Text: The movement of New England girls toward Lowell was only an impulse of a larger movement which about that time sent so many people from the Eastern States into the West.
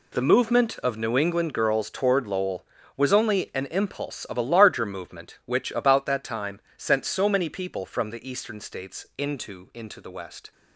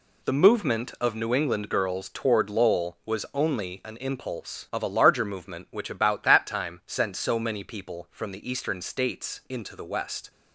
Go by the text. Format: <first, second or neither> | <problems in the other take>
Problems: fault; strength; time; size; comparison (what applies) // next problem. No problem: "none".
second | pauses between "time" and "sent"; slight; at 6.6 s; 0.16 s long // says "into" twice; at 9.7 s